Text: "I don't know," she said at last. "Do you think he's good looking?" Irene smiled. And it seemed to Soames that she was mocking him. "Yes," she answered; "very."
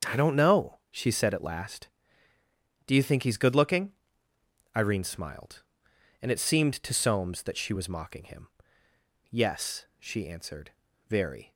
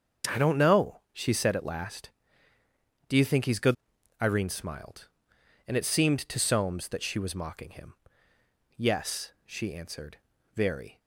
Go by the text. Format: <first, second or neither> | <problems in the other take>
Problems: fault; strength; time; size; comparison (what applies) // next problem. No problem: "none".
first | starts louder than the rest; until 1.4 s; 6.5 dB; also in the first // skips "looking"; at 3.9 s